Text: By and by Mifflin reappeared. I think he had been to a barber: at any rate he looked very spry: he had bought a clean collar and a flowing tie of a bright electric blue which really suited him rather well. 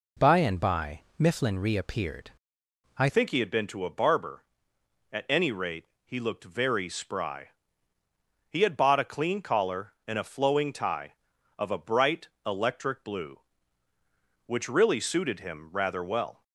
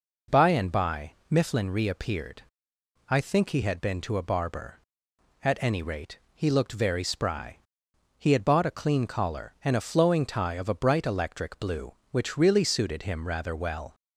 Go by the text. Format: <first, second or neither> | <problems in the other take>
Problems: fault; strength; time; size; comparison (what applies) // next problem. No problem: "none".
second | pauses between "by" and "Mifflin"; slight; at 1.0 s; 0.18 s long; slight in the second // changes voice at "think"; from 3.0 s on; 13.4 s long // pauses between "rate" and "he"; slight; at 5.8 s; 0.18 s long; slight in the second // pauses between "bright" and "electric"; slight; at 12.2 s; 0.18 s long